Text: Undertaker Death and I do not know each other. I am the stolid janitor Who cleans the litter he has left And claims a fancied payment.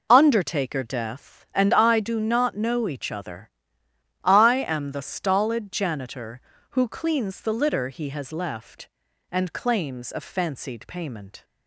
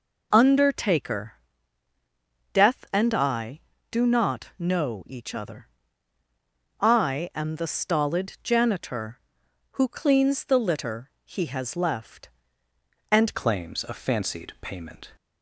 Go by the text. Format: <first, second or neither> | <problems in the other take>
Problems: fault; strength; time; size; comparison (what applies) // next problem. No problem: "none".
first | pauses between "Undertaker" and "Death"; at 1.3 s; 1.2 s long // changes voice at "claims"; from 13.3 s on; 1.8 s long